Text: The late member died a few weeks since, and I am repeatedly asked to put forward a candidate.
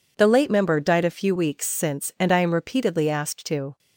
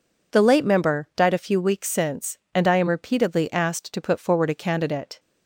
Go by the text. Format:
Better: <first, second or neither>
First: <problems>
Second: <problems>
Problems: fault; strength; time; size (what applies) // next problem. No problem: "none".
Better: second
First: stops before "put forward a candidate"; at 3.7 s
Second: none